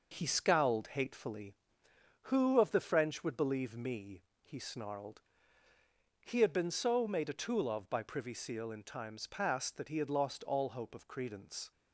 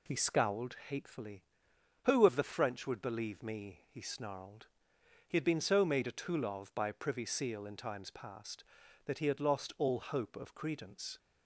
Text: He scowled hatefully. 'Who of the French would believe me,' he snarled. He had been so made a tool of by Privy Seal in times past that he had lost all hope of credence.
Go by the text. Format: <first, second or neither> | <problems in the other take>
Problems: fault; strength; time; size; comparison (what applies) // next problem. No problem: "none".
second | gets quieter; noticeable; throughout; 5.5 dB